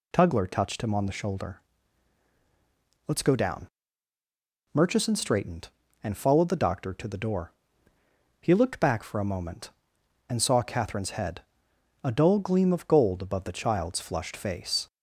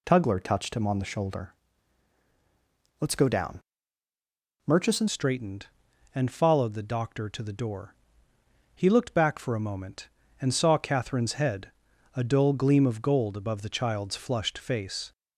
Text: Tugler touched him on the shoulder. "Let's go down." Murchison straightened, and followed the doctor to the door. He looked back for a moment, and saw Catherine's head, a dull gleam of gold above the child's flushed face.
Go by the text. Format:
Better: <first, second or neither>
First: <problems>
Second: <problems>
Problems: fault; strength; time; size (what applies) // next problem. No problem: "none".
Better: first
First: none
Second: changes voice at "straightened"; from 5.0 s on; 10.1 s long